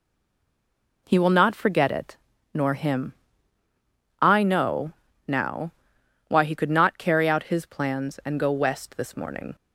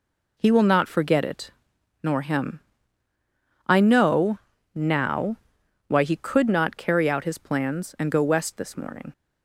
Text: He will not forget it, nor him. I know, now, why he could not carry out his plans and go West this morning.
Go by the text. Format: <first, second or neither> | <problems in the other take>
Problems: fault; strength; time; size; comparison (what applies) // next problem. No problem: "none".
second | stays silent before the first word; until 1.0 s; 1.0 s long